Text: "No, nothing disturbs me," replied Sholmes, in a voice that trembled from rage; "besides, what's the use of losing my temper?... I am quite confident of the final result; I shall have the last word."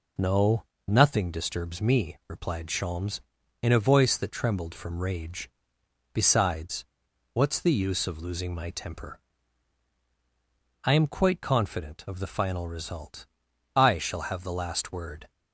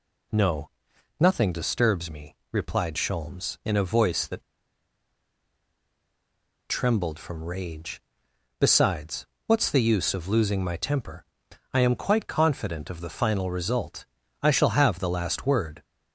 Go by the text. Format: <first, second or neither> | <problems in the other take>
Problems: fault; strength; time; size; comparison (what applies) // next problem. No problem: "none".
first | pauses between "that" and "trembled"; strong; at 4.4 s; 2.2 s long